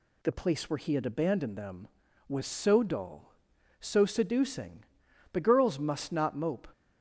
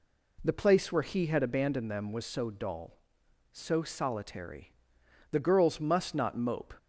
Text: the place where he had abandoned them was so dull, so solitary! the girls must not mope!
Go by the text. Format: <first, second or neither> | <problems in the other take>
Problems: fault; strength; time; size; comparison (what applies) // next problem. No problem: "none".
second | says "seducing" for "solitary"; at 4.0 s